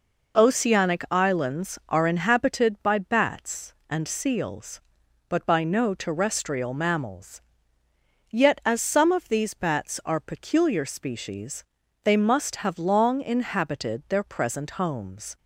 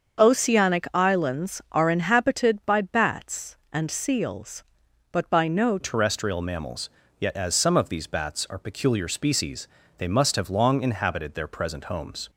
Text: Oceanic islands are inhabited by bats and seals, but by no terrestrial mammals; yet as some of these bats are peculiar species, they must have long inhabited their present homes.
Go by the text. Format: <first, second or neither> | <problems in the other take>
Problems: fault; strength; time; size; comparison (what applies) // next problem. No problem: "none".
first | starts louder than the rest; until 1.2 s; 6.5 dB // changes voice at "terrestrial"; from 5.8 s on; 6.4 s long